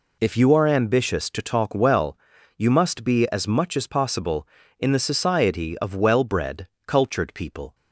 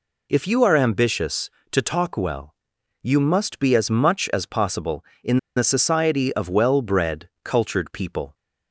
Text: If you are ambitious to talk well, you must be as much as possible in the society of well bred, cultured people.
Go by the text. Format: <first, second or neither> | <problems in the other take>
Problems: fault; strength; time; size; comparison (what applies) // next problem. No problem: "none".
first | pauses between "in" and "the"; slight; at 5.3 s; 0.18 s long